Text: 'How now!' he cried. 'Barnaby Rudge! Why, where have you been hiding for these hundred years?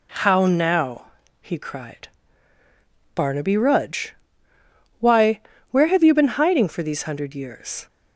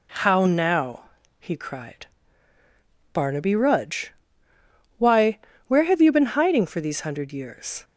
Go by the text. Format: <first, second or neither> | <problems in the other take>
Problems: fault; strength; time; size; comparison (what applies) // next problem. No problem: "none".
neither | none